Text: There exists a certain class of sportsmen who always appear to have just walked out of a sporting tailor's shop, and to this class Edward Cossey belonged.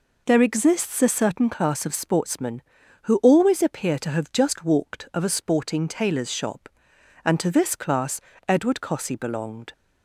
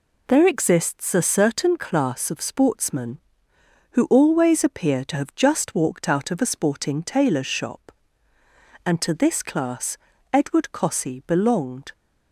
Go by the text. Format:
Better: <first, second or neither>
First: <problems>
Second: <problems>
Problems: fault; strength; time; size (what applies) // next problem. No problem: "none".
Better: second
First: skips "out"; at 5.1 s // pauses between "class" and "Edward"; slight; at 8.1 s; 0.26 s long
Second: pauses between "class" and "Edward"; slight; at 9.9 s; 0.36 s long